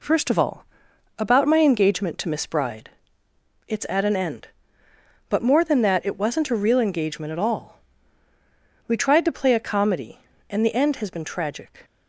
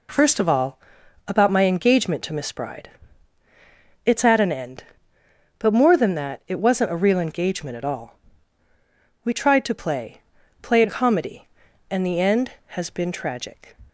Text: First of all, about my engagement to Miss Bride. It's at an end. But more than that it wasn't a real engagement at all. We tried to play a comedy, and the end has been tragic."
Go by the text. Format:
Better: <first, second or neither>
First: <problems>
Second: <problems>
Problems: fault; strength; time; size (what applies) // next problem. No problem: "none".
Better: first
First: none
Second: says "play" twice; at 10.6 s